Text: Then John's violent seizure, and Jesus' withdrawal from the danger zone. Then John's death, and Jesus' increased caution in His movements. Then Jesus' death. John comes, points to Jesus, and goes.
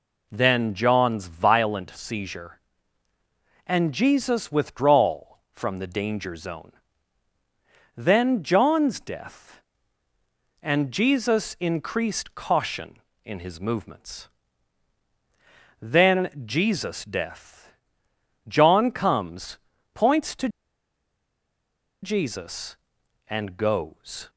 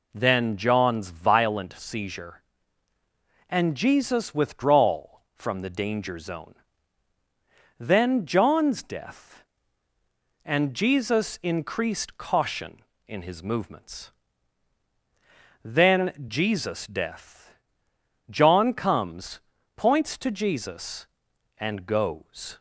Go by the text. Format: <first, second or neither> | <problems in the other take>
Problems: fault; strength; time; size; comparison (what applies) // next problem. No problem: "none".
second | pauses between "to" and "Jesus"; strong; at 20.4 s; 1.5 s long